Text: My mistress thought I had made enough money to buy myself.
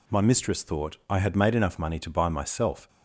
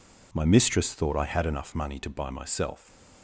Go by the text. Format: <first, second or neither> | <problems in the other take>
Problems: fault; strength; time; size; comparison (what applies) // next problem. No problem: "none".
first | skips "made"; at 1.4 s